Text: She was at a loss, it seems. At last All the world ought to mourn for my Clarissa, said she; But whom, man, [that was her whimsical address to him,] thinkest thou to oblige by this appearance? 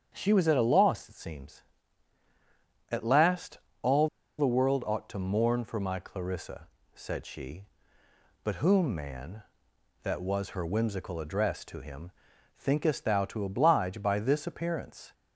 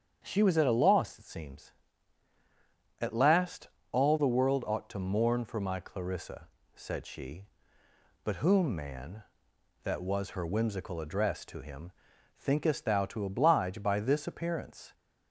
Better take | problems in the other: second | starts louder than the rest; strong; until 1.1 s; 8 dB; strong in the second // pauses between "last" and "All"; slight; at 3.5 s; 0.24 s long; slight in the second // pauses between "All" and "the"; slight; at 4.0 s; 0.31 s long

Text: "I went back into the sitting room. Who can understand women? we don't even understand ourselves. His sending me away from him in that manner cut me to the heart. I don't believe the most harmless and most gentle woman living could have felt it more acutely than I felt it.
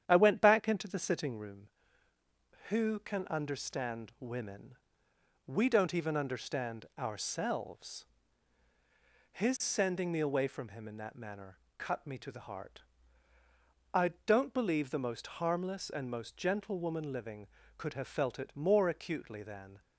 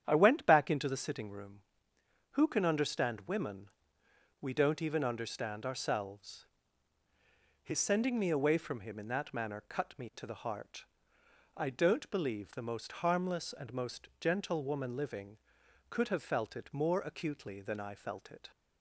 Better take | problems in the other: second | starts louder than the rest; strong; until 1.0 s; 9.5 dB; strong in the second // pauses between "manner" and "cut"; slight; at 11.5 s; 0.22 s long // stops before "I felt it"; at 19.8 s

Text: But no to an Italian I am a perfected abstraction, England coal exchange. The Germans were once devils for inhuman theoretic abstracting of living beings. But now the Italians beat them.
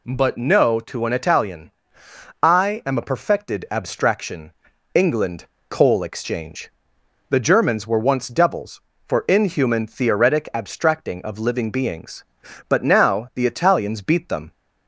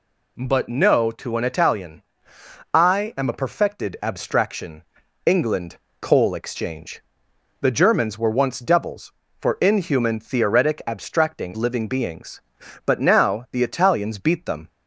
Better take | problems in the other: first | pauses between "Italian" and "I"; noticeable; at 2.0 s; 0.68 s long; noticeable in the first // pauses between "England" and "coal"; slight; at 5.7 s; 0.22 s long; slight in the first // skips "of"; at 11.5 s

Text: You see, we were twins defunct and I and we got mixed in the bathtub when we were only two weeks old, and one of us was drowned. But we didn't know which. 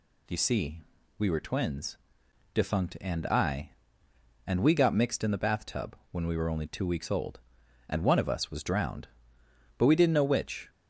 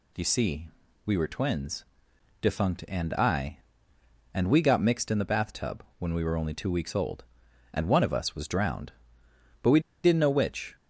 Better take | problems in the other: first | pauses between "twins" and "defunct"; noticeable; at 1.8 s; 0.56 s long; noticeable in the first // pauses between "bathtub" and "when"; slight; at 5.8 s; 0.16 s long; slight in the first // pauses between "we" and "didn't"; slight; at 9.7 s; 0.24 s long

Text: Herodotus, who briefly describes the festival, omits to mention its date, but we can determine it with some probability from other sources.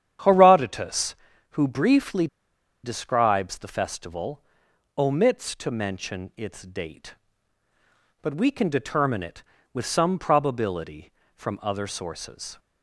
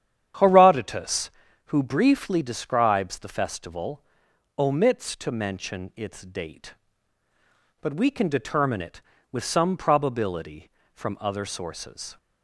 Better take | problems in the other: second | starts louder than the rest; strong; until 1.6 s; 9.5 dB; strong in the second // pauses between "briefly" and "describes"; noticeable; at 2.2 s; 0.57 s long

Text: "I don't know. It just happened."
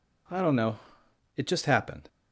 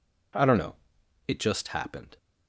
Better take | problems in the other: neither | none

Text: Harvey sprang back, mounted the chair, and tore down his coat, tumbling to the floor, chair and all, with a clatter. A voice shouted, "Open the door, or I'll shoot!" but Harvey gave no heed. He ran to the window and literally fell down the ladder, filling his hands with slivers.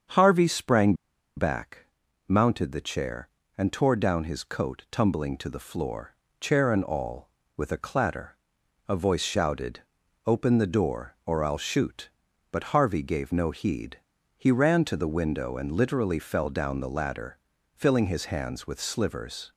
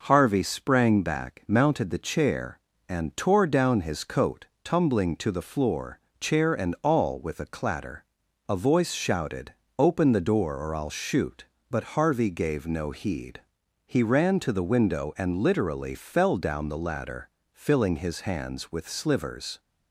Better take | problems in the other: second | starts louder than the rest; strong; until 1.5 s; 7 dB // pauses between "sprang" and "back"; at 0.9 s; 0.42 s long

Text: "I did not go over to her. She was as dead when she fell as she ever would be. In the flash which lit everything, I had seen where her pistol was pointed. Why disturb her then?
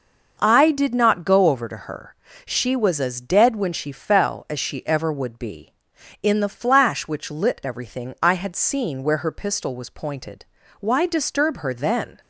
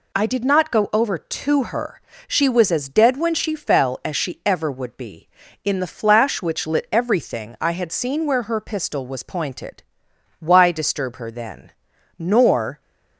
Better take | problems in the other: first | goes on to say "Nor"; noticeable; from 12.1 s on; 0.62 s long

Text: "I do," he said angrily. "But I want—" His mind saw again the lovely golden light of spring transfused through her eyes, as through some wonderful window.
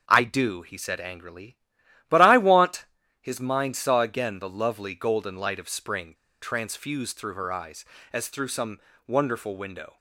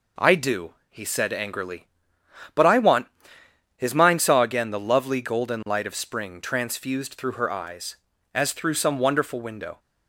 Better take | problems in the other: second | starts louder than the rest; until 1.0 s; 7 dB // pauses between "spring" and "transfused"; slight; at 6.1 s; 0.27 s long // pauses between "some" and "wonderful"; slight; at 8.7 s; 0.30 s long

